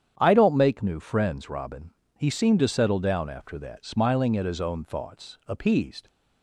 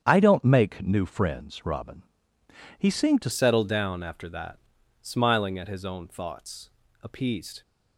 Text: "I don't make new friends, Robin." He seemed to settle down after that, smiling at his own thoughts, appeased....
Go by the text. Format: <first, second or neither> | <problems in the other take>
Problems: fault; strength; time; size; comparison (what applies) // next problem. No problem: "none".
first | starts louder than the rest; strong; until 1.0 s; 8.5 dB; strong in the first // changes voice at "settle"; from 3.3 s on; 4.3 s long